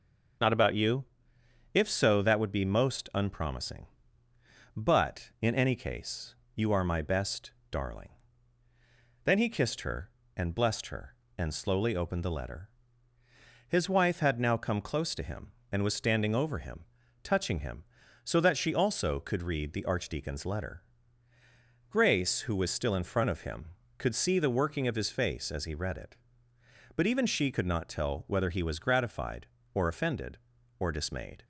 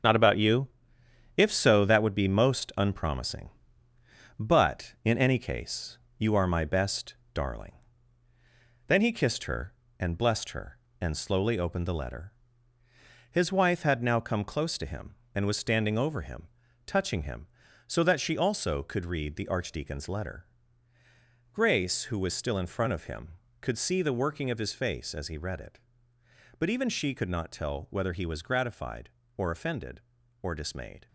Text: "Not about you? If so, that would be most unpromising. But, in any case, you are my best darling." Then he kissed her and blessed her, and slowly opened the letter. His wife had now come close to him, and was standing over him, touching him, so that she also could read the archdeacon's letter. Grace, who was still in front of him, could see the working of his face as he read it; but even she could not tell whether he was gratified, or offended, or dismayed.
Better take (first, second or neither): first